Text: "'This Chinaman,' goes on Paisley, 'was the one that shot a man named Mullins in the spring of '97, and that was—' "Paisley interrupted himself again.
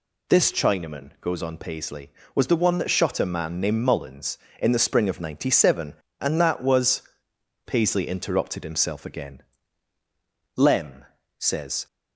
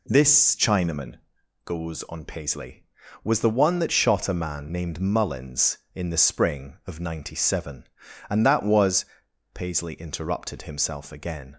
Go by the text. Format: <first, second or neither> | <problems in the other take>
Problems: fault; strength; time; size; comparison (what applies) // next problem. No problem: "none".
second | goes on to say "Lem says"; from 10.5 s on; 1.3 s long